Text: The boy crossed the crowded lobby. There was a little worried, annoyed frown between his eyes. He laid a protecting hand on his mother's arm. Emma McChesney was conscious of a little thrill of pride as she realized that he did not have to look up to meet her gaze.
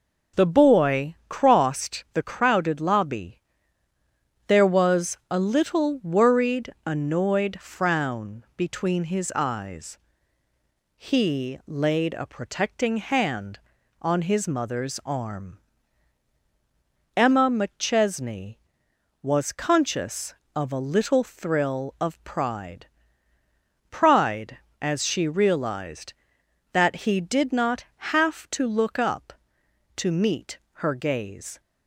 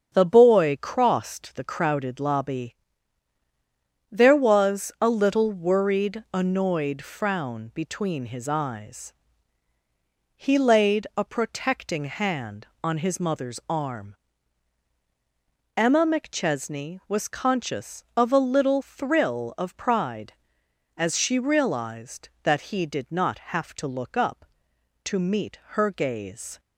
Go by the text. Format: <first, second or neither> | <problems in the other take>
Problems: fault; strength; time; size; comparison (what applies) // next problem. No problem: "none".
second | starts louder than the rest; until 1.5 s; 6.5 dB; strong in the second // says "pride" twice; at 23.8 s // pauses between "meet" and "her"; slight; at 30.5 s; 0.18 s long